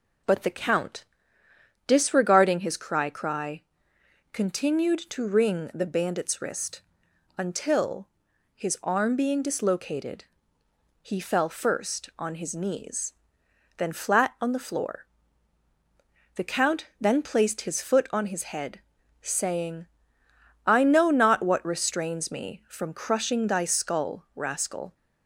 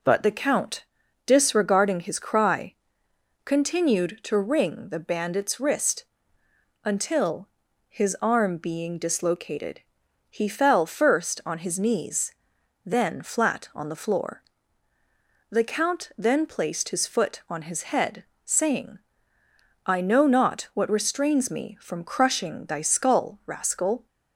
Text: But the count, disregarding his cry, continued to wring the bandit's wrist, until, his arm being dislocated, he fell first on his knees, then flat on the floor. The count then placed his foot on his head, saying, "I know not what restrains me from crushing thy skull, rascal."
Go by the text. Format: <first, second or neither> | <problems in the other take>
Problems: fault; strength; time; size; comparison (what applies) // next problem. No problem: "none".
second | says "cry" twice; at 3.0 s